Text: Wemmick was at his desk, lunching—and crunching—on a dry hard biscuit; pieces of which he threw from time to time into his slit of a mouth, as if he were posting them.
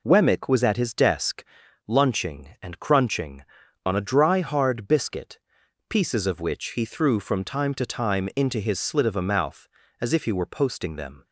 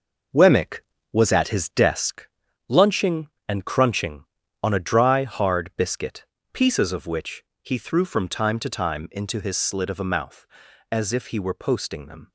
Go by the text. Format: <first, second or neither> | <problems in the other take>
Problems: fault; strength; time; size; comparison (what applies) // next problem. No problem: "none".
first | gets quieter; strong; throughout; 8.5 dB // pauses between "which" and "he"; slight; at 7.4 s; 0.20 s long